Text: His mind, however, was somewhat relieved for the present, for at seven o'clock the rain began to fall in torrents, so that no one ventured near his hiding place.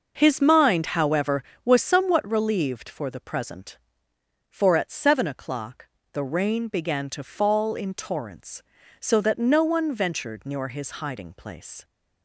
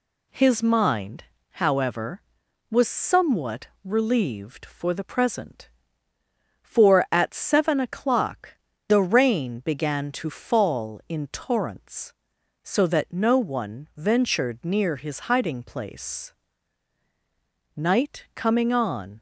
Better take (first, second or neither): first